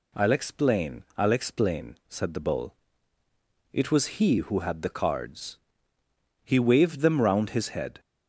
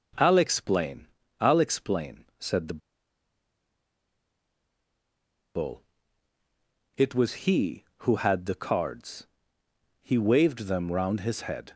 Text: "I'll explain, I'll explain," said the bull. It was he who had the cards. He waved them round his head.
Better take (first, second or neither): first